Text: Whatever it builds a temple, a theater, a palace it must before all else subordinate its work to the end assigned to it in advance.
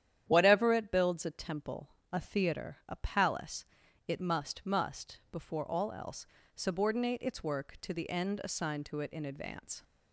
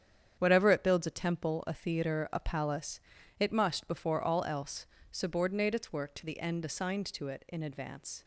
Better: second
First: starts louder than the rest; strong; until 1.2 s; 10 dB // pauses between "palace" and "it"; noticeable; at 3.6 s; 0.46 s long // says "must" twice; at 4.6 s // pauses between "else" and "subordinate"; slight; at 6.2 s; 0.28 s long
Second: starts louder than the rest; strong; until 1.4 s; 8.5 dB // pauses between "palace" and "it"; at 2.9 s; 0.40 s long // pauses between "else" and "subordinate"; slight; at 4.8 s; 0.26 s long

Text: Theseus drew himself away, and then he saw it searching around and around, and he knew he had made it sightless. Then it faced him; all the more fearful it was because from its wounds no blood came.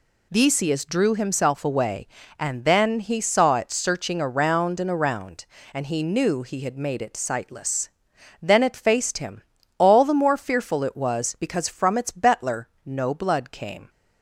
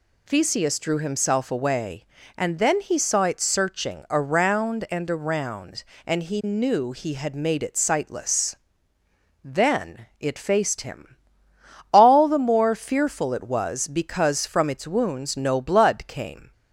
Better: second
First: says "betler" for "wounds"; at 12.0 s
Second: none

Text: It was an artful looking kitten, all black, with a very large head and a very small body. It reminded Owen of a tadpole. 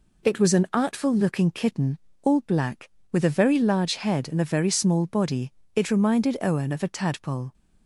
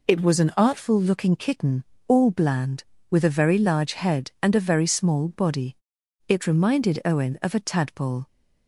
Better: first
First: none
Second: says "bland" for "black"; at 2.3 s

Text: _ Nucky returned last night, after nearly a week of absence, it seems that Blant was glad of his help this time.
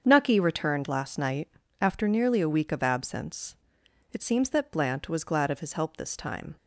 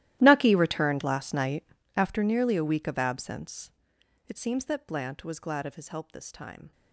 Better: first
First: starts louder than the rest; until 1.0 s; 7 dB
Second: gets quieter; strong; throughout; 21 dB // starts louder than the rest; strong; until 1.2 s; 14.5 dB

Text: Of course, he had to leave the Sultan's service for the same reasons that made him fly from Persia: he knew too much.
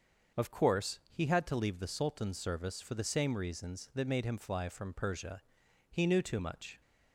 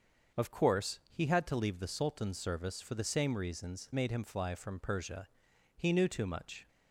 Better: first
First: starts louder than the rest; until 1.4 s; 6.5 dB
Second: starts louder than the rest; until 1.5 s; 6.5 dB // skips "that"; at 3.9 s

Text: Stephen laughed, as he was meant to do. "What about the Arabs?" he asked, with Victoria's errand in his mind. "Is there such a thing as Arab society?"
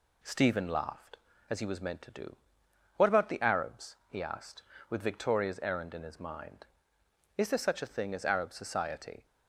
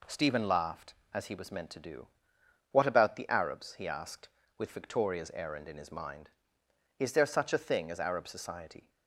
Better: neither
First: none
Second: none

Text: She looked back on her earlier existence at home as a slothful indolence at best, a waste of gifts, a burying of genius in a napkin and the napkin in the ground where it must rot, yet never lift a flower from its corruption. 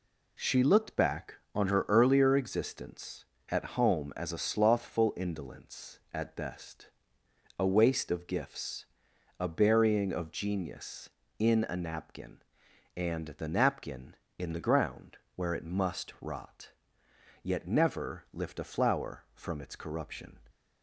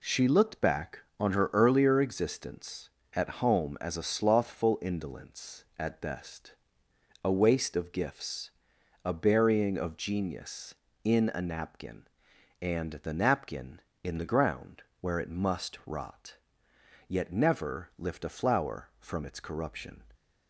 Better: neither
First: pauses between "ground" and "where"; slight; at 15.1 s; 0.16 s long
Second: pauses between "ground" and "where"; slight; at 14.8 s; 0.16 s long

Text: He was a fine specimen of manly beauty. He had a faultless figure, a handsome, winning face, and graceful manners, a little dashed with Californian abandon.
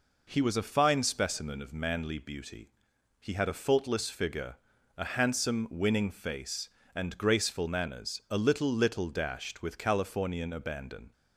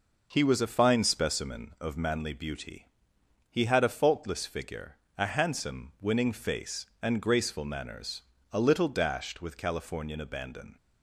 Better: second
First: says "little" twice; at 8.7 s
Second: none

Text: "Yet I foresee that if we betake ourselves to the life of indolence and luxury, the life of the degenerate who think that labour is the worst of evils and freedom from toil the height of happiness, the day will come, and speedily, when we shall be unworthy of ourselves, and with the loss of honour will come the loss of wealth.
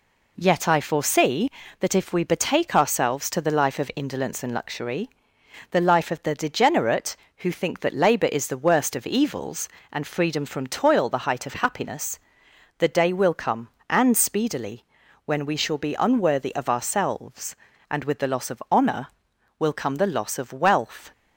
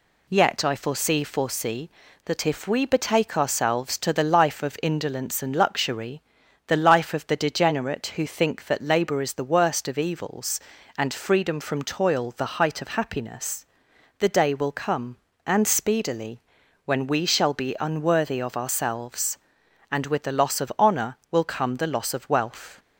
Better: first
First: none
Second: says "foresee" twice; at 1.2 s

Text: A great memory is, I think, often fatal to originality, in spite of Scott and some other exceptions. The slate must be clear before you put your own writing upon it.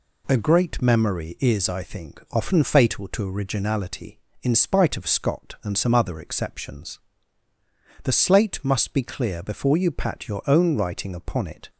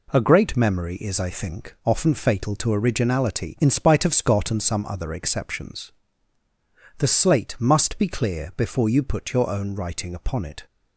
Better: second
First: says "pat" for "put"; at 9.9 s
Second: none

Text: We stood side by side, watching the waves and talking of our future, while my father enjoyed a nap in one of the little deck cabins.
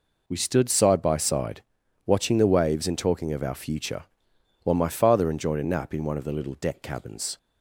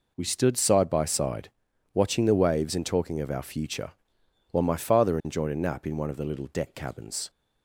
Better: neither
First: none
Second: none

